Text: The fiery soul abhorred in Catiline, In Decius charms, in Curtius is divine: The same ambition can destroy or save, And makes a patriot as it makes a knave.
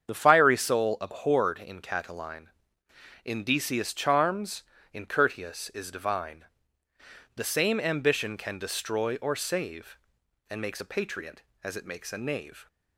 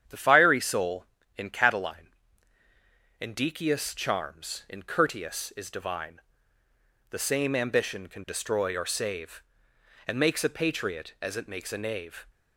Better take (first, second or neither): first